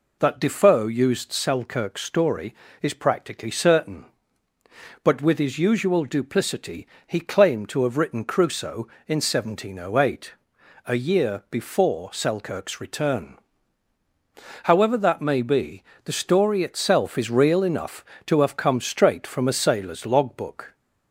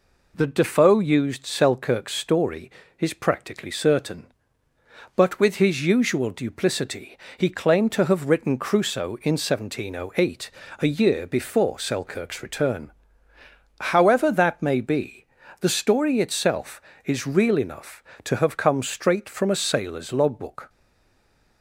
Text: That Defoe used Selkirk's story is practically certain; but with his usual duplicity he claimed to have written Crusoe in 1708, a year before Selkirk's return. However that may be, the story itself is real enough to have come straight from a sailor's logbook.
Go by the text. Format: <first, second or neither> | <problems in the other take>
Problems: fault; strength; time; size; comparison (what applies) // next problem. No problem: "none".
first | pauses between "duplicity" and "he"; slight; at 7.1 s; 0.20 s long; slight in the first // stays silent after the last word; slight; from 20.6 s on; 1.0 s long